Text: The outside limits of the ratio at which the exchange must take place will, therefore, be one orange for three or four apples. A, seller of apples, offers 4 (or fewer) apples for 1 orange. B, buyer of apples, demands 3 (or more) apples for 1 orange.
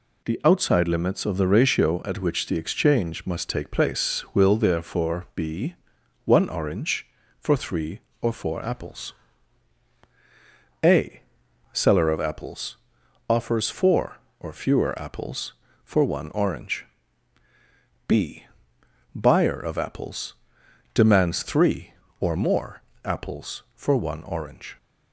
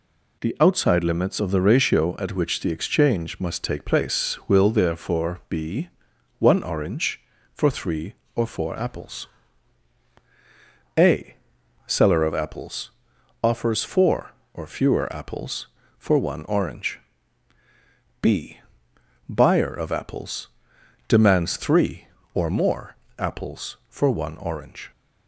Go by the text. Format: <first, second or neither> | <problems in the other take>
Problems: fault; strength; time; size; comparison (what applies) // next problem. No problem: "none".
neither | pauses between "be" and "one"; noticeable; the same in both